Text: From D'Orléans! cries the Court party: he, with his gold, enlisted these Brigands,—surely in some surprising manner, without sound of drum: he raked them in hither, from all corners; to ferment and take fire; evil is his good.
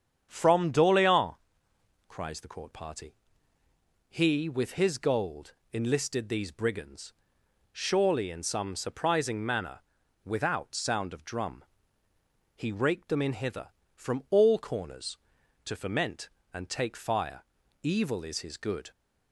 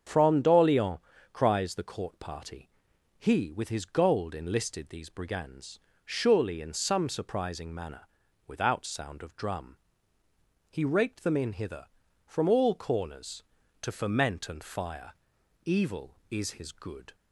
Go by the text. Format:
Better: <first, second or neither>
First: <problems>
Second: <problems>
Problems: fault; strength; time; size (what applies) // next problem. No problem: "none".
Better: first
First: starts louder than the rest; strong; until 1.3 s; 8 dB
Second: starts louder than the rest; strong; until 1.4 s; 7.5 dB // skips "take"; at 14.6 s